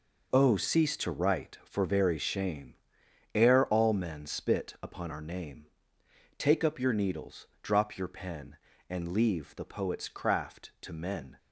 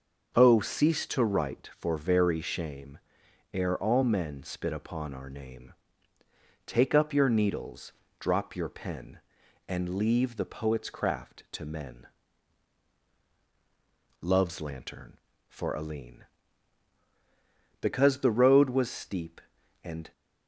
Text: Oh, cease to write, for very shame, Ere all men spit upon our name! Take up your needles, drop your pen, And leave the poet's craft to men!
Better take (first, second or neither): first